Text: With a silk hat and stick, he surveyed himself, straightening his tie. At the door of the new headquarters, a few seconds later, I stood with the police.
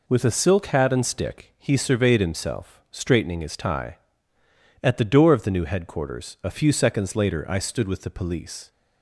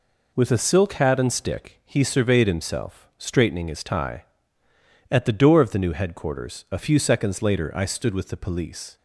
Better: neither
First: none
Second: none

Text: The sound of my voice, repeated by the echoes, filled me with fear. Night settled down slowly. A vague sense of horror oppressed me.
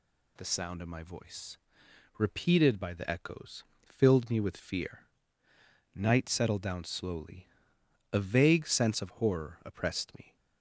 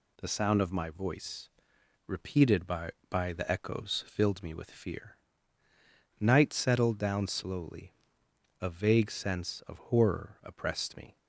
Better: first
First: none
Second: says "by" twice; at 3.0 s

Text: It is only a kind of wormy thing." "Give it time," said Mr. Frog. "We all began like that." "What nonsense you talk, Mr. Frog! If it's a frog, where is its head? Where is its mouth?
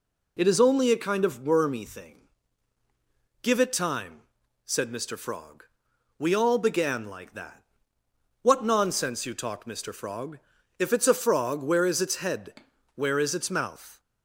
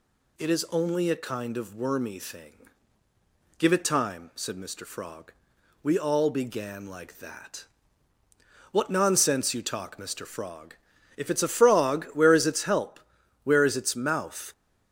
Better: first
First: none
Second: says "help" for "head"; at 12.6 s

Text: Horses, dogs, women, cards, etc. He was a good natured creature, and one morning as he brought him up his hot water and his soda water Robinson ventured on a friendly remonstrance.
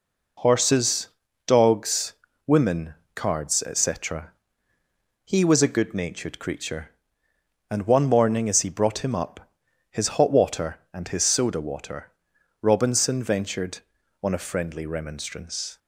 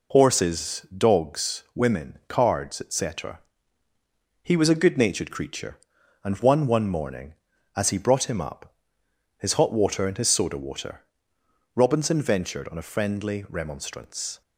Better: first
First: pauses between "up" and "his"; at 9.5 s; 0.40 s long // pauses between "water" and "Robinson"; noticeable; at 12.1 s; 0.50 s long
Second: says "one" twice; at 6.6 s // pauses between "up" and "his"; noticeable; at 8.7 s; 0.64 s long // pauses between "water" and "Robinson"; noticeable; at 11.0 s; 0.72 s long

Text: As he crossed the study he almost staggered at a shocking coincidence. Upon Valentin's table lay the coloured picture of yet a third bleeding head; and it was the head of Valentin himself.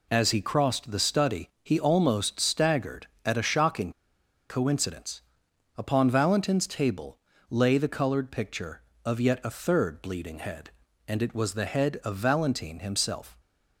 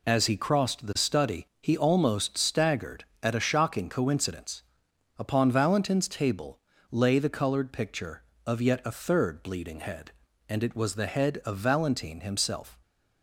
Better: second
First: pauses between "study" and "he"; slight; at 1.4 s; 0.16 s long // pauses between "shocking" and "coincidence"; noticeable; at 3.9 s; 0.59 s long // pauses between "table" and "lay"; slight; at 7.1 s; 0.32 s long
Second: pauses between "study" and "he"; slight; at 1.4 s; 0.16 s long // pauses between "table" and "lay"; slight; at 6.5 s; 0.32 s long

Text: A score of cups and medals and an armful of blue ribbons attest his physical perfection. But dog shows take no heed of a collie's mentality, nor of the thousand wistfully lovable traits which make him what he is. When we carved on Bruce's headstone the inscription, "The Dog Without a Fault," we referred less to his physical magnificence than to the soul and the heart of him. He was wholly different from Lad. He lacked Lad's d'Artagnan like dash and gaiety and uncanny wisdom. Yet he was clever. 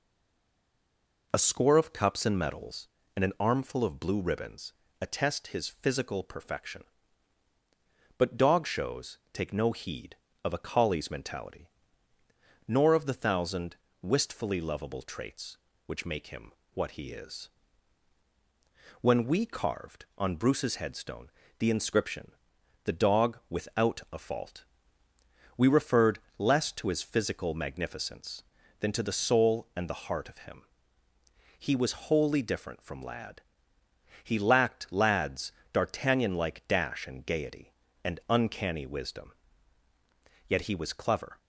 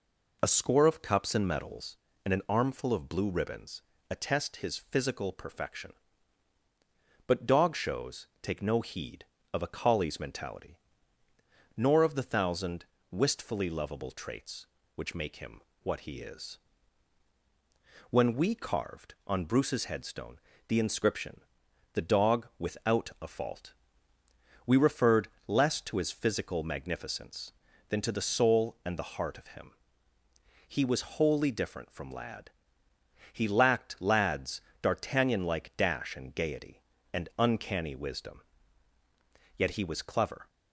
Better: second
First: stays silent before the first word; noticeable; until 1.3 s; 1.3 s long // pauses between "ribbons" and "attest"; slight; at 4.7 s; 0.28 s long // pauses between "thousand" and "wistfully"; slight; at 13.7 s; 0.26 s long // pauses between "him" and "what"; slight; at 16.5 s; 0.24 s long // pauses between "headstone" and "the"; slight; at 21.3 s; 0.28 s long // pauses between "referred" and "less"; slight; at 26.1 s; 0.20 s long // pauses between "Lad's" and "d'Artagnan"; slight; at 35.5 s; 0.22 s long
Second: pauses between "ribbons" and "attest"; slight; at 3.8 s; 0.28 s long // pauses between "thousand" and "wistfully"; slight; at 12.8 s; 0.26 s long // pauses between "him" and "what"; slight; at 15.5 s; 0.24 s long // pauses between "headstone" and "the"; slight; at 20.3 s; 0.28 s long // pauses between "referred" and "less"; slight; at 25.2 s; 0.20 s long // pauses between "Lad's" and "d'Artagnan"; slight; at 34.6 s; 0.22 s long

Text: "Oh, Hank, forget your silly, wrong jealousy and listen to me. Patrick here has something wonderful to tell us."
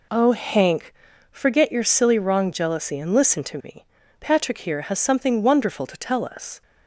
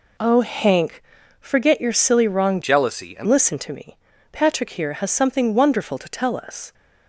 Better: first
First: none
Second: changes voice from "jealousy" to "and"; from 2.6 to 3.2 s; 0.6 s long

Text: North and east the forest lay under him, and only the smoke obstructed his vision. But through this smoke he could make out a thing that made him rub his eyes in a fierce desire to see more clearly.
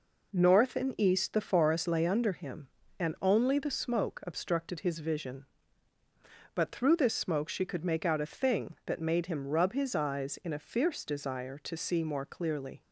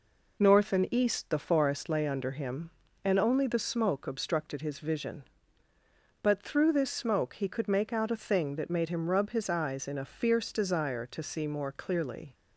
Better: second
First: says "she" for "he"; at 7.4 s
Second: none

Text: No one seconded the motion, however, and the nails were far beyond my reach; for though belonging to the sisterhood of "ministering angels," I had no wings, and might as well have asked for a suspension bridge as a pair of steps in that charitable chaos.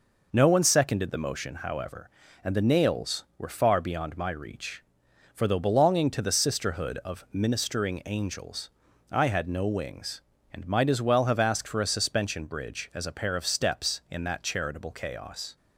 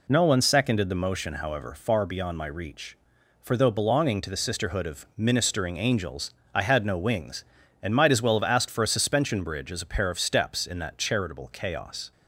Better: first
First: none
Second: skips "and the nails were"; at 1.7 s

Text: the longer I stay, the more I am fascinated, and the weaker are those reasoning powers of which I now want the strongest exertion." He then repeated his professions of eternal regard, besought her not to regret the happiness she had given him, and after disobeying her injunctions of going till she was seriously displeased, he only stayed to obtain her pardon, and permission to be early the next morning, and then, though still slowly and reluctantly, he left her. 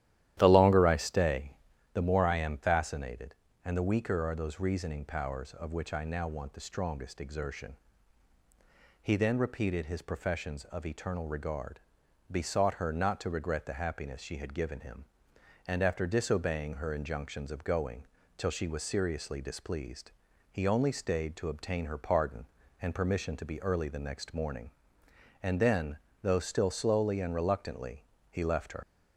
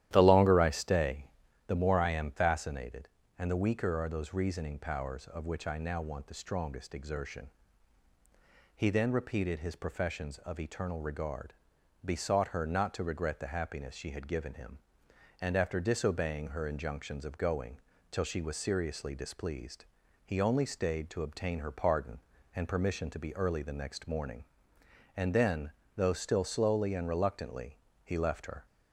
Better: second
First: starts louder than the rest; strong; until 1.3 s; 12.5 dB // pauses between "going" and "till"; slight; at 18.0 s; 0.30 s long // leaves "her" unfinished; at 28.8 s; 90 ms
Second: starts louder than the rest; strong; until 1.1 s; 12.5 dB // pauses between "going" and "till"; slight; at 17.7 s; 0.30 s long

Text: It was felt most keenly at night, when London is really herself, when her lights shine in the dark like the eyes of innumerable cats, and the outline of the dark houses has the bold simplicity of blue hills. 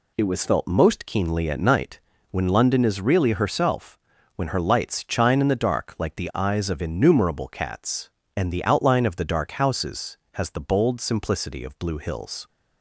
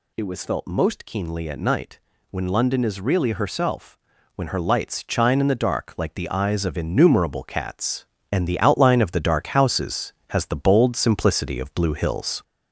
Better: first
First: none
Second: gets louder; noticeable; throughout; 4 dB

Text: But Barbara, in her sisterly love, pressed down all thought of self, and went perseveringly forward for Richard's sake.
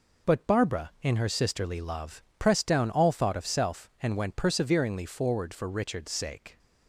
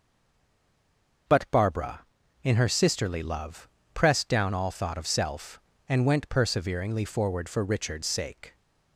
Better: first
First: none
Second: stays silent before the first word; noticeable; until 1.2 s; 1.2 s long

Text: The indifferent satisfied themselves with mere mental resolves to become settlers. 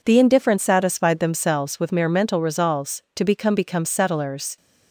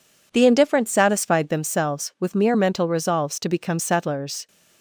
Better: second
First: says "become" twice; at 3.5 s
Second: none

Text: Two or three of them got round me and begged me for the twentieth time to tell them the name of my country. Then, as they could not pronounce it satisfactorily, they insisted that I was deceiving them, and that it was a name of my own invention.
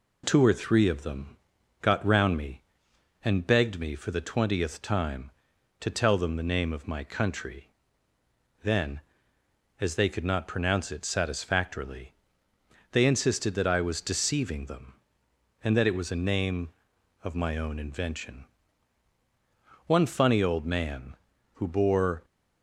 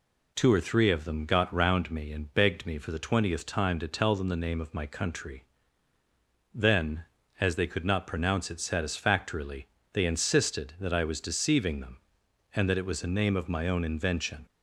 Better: second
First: pauses between "them" and "got"; noticeable; at 1.3 s; 0.46 s long // goes on to say "One funny old man who bore"; strong; from 19.8 s on; 2.3 s long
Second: none

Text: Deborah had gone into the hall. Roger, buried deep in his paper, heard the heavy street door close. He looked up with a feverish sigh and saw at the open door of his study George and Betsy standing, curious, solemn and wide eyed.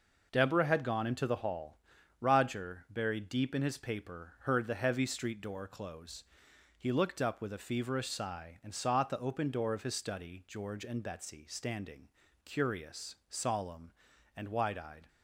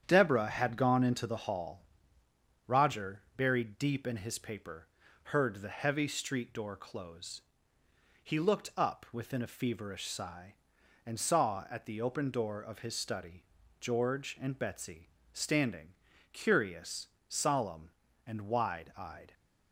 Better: first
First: none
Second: starts louder than the rest; strong; until 1.0 s; 9 dB // says "within" for "with"; at 9.1 s // pauses between "study" and "George"; slight; at 13.4 s; 0.36 s long // pauses between "Betsy" and "standing"; slight; at 15.0 s; 0.26 s long

